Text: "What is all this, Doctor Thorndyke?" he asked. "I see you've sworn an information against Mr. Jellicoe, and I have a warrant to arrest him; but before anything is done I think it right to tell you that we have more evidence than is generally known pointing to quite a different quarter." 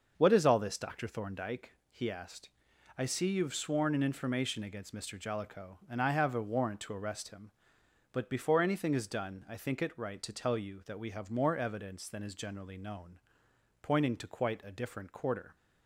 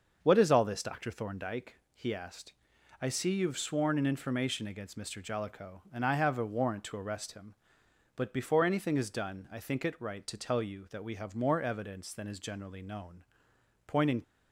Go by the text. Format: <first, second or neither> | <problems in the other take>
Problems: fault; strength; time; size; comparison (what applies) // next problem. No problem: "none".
first | starts louder than the rest; until 1.2 s; 6.5 dB; also in the first // pauses between "known" and "pointing"; noticeable; at 13.2 s; 0.60 s long; noticeable in the first // stops before "to quite a different quarter"; at 14.2 s